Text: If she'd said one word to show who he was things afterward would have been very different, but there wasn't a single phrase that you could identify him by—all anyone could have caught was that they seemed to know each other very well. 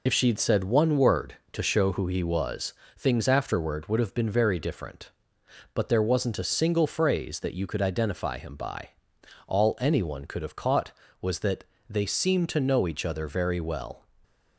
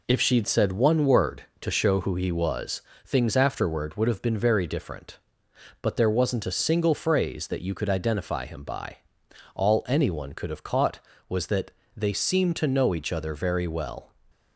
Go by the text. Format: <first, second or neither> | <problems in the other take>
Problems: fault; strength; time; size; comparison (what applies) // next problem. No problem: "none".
second | loses the start of "If"; at 0.0 s; 60 ms // pauses between "was" and "things"; slight; at 2.7 s; 0.24 s long; slight in the second // pauses between "that" and "they"; slight; at 11.6 s; 0.24 s long; slight in the second